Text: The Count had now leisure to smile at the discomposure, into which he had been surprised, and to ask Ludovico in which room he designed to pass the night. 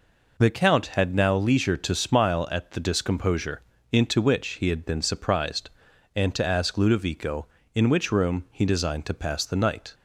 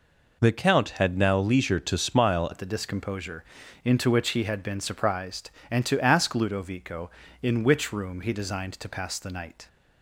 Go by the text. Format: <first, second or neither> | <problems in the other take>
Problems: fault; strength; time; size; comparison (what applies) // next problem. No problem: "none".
first | changes voice at "at"; from 2.5 s on; 7.1 s long